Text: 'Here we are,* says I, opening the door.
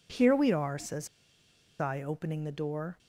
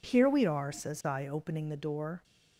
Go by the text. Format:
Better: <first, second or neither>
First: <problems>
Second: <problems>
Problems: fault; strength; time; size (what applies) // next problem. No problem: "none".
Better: second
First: pauses between "says" and "I"; noticeable; at 1.0 s; 0.72 s long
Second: none